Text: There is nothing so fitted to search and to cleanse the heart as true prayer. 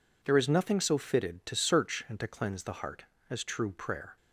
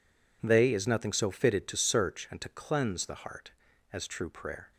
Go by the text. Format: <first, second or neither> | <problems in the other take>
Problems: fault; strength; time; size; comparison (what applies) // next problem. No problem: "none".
first | says "They" for "There"; at 0.4 s